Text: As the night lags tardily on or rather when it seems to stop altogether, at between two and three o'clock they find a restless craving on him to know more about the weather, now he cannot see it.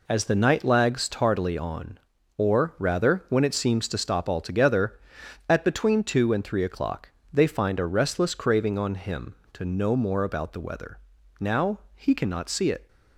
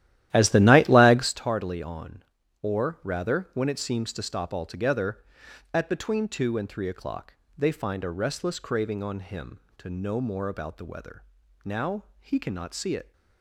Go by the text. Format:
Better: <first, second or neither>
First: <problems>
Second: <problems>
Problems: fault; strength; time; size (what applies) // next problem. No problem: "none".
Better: first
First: pauses between "o'clock" and "they"; slight; at 7.0 s; 0.22 s long // pauses between "now" and "he"; slight; at 11.7 s; 0.16 s long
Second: starts louder than the rest; strong; until 1.4 s; 13 dB // pauses between "o'clock" and "they"; slight; at 7.3 s; 0.22 s long // pauses between "now" and "he"; slight; at 12.0 s; 0.16 s long